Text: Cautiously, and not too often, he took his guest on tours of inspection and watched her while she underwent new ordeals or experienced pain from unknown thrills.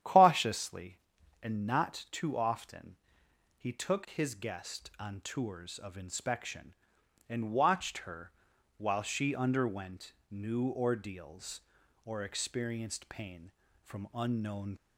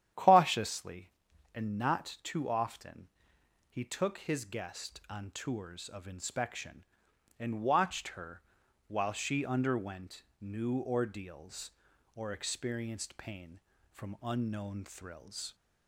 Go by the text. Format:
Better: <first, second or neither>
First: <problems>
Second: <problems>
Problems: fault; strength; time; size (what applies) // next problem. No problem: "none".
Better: second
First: starts louder than the rest; strong; until 1.4 s; 10.5 dB // pauses between "her" and "while"; noticeable; at 8.3 s; 0.46 s long // pauses between "underwent" and "new"; slight; at 10.1 s; 0.18 s long // stops before "thrills"; at 14.7 s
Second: starts louder than the rest; strong; until 1.5 s; 10.5 dB // pauses between "her" and "while"; noticeable; at 8.4 s; 0.46 s long // pauses between "underwent" and "new"; slight; at 10.2 s; 0.18 s long